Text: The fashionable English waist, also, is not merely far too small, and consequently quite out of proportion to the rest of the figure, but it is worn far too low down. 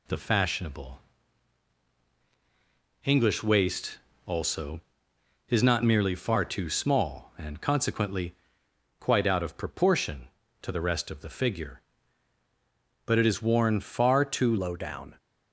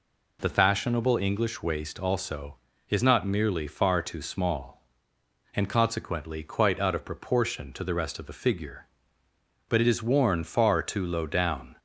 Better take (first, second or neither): second